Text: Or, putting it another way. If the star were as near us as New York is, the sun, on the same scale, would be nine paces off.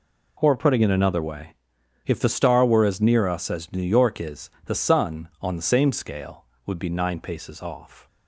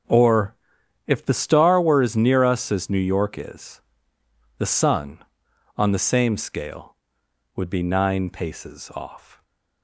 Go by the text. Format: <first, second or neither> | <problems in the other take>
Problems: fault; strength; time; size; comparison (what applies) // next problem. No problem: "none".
first | starts louder than the rest; until 1.6 s; 6.5 dB // skips "putting it another way"; at 0.8 s